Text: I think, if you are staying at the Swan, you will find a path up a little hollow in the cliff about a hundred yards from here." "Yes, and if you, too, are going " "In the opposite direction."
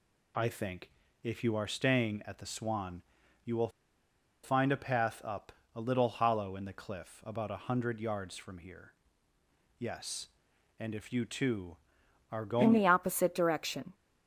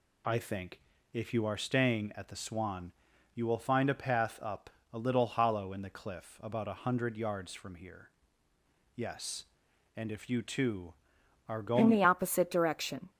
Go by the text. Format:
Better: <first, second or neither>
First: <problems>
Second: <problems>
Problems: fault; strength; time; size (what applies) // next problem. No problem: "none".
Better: second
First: pauses between "will" and "find"; noticeable; at 3.6 s; 0.73 s long // pauses between "up" and "a"; slight; at 5.5 s; 0.22 s long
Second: pauses between "up" and "a"; slight; at 4.6 s; 0.22 s long